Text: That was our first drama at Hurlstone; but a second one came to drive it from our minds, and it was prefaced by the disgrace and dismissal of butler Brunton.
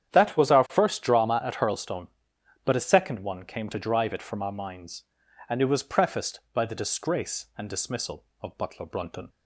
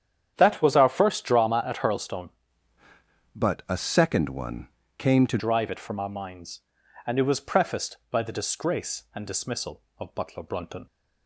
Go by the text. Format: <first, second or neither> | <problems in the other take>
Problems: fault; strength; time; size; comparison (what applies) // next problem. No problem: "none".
first | starts louder than the rest; strong; until 1.3 s; 9 dB; strong in the first // changes voice from "but" to "to"; from 3.3 to 5.3 s; 2.0 s long // pauses between "one" and "came"; slight; at 4.6 s; 0.30 s long